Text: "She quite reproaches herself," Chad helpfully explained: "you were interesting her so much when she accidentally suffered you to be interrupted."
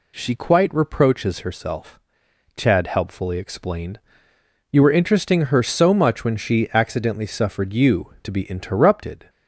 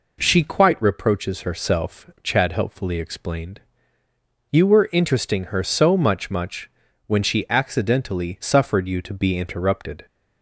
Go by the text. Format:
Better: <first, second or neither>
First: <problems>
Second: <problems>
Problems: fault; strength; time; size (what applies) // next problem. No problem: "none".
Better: first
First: none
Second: says "much" twice; at 6.2 s